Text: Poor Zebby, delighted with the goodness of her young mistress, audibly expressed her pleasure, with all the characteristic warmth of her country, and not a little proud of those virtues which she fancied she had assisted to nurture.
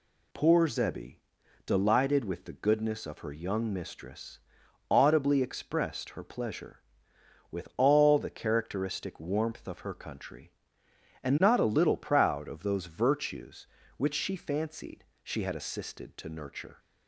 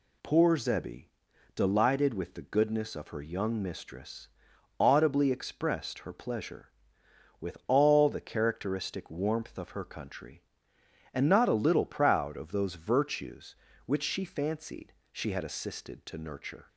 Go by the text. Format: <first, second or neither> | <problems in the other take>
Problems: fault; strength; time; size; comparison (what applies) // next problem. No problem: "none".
neither | pauses between "fancied" and "she"; slight; the same in both